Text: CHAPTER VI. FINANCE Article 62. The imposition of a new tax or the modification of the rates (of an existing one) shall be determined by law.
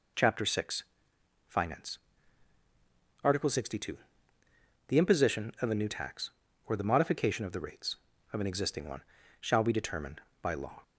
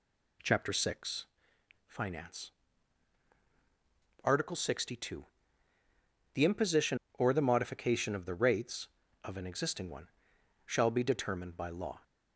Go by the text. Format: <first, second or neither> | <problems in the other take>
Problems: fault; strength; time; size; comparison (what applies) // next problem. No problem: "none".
first | pauses between "FINANCE" and "Article"; strong; at 2.5 s; 1.7 s long; strong in the first // skips "of a new tax"; at 7.0 s